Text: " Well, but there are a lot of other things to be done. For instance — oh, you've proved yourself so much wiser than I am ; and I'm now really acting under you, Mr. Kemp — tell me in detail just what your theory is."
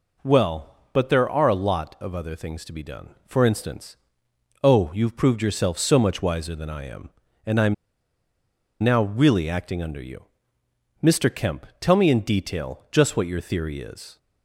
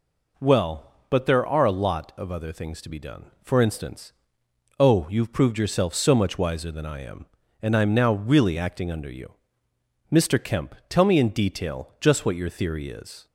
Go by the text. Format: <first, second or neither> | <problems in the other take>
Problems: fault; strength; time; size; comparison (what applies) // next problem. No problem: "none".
second | pauses between "I'm" and "now"; at 7.7 s; 1.0 s long